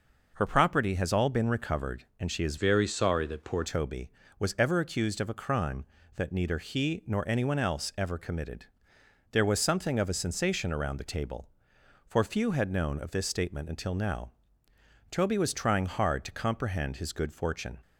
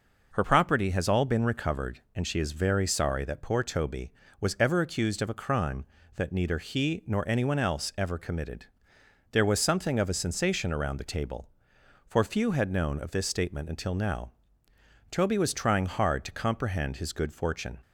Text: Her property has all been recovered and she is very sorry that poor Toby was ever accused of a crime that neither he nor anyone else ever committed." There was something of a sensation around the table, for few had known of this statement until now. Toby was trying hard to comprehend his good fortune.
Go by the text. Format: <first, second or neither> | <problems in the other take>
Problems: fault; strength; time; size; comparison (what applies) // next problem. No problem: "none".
second | changes voice from "very" to "poor"; from 2.5 to 3.6 s; 1.1 s long